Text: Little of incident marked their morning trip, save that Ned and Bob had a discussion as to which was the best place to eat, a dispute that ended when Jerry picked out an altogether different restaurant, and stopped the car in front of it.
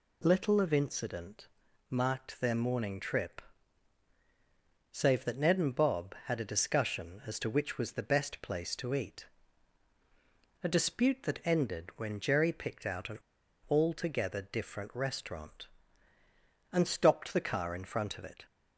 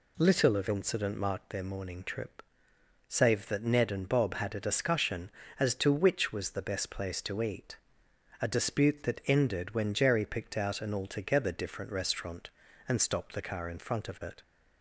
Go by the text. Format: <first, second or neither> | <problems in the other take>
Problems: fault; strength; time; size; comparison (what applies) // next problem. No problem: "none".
second | pauses between "incident" and "marked"; at 1.4 s; 0.42 s long // pauses between "an" and "altogether"; noticeable; at 13.1 s; 0.50 s long